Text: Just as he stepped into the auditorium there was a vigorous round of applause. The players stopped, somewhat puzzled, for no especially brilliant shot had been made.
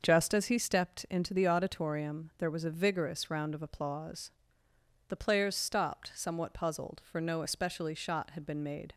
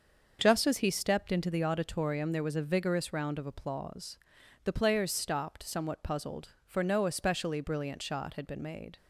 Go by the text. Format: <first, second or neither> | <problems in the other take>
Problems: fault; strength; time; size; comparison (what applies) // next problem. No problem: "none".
second | starts louder than the rest; until 1.0 s; 6 dB; also in the second // skips "brilliant"; at 7.9 s